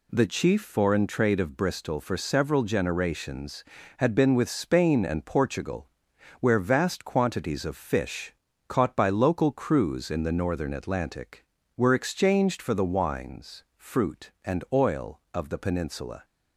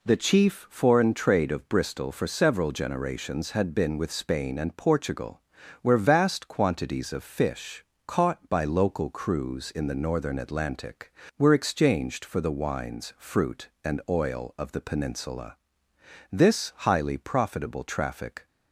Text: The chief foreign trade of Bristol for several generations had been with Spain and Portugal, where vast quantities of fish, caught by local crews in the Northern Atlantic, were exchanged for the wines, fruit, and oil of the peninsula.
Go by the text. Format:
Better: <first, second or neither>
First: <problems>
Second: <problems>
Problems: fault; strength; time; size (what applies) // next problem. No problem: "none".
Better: first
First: none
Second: goes on to say "This highly profitable traffic"; strong; from 16.3 s on; 2.1 s long